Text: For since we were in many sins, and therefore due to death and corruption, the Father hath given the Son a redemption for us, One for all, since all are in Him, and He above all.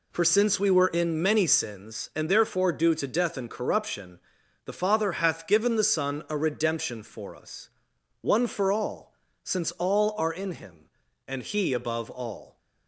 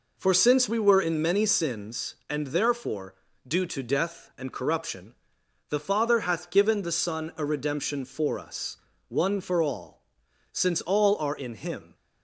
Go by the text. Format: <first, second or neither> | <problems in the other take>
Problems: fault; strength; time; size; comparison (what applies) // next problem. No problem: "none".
first | pauses between "therefore" and "due"; slight; at 3.1 s; 0.32 s long // stops before "and He above all"; at 11.9 s